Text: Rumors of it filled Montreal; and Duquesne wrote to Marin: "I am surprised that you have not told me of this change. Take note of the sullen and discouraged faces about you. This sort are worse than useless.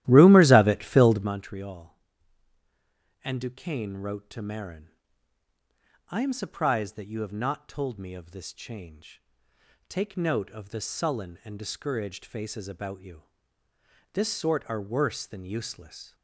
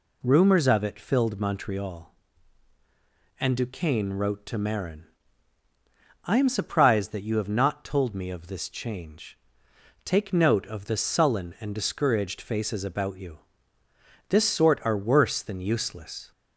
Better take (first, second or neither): second